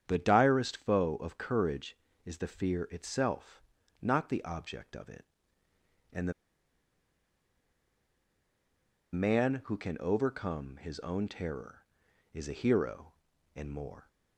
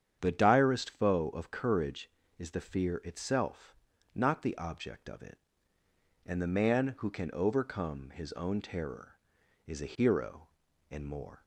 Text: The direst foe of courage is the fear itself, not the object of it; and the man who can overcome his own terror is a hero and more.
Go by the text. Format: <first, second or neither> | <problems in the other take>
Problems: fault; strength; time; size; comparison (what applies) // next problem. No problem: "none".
second | starts louder than the rest; strong; until 1.0 s; 8.5 dB; strong in the second // pauses between "the" and "man"; strong; at 6.3 s; 2.8 s long